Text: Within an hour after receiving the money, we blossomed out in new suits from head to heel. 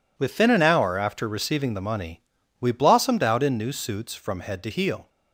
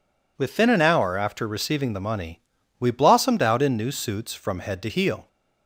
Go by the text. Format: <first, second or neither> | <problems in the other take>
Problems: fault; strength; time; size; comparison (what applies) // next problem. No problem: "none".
second | gets quieter; strong; throughout; 11.5 dB